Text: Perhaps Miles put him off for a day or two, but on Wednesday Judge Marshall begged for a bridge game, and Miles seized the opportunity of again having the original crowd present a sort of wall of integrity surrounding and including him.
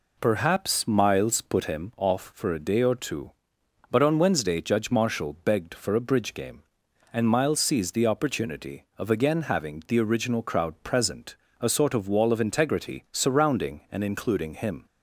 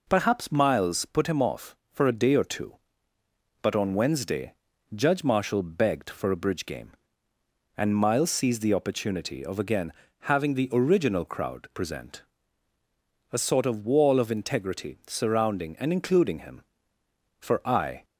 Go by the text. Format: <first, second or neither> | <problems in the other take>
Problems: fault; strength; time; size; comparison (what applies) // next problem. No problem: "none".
first | pauses between "Wednesday" and "Judge"; at 4.5 s; 0.42 s long // pauses between "again" and "having"; slight; at 9.9 s; 0.28 s long // pauses between "present" and "a"; at 12.2 s; 1.1 s long; slight in the first // goes on to say "For I"; noticeable; from 17.3 s on; 0.66 s long